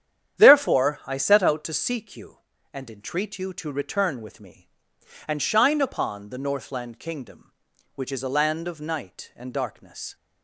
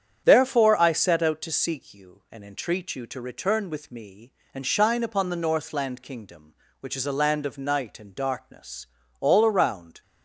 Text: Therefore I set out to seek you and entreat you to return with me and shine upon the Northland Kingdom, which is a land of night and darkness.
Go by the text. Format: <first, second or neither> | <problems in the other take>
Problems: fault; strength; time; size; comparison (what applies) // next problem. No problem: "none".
first | starts louder than the rest; strong; until 1.2 s; 8.5 dB; strong in the first // goes on to say "All around"; noticeable; from 9.1 s on; 0.82 s long